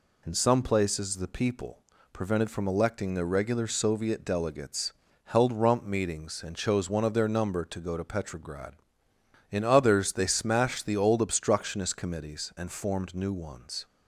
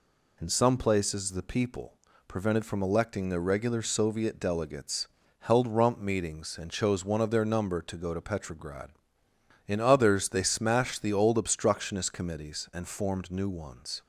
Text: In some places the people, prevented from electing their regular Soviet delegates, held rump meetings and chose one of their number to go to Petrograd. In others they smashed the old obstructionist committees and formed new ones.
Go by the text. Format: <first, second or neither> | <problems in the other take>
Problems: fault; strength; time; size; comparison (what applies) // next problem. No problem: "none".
neither | none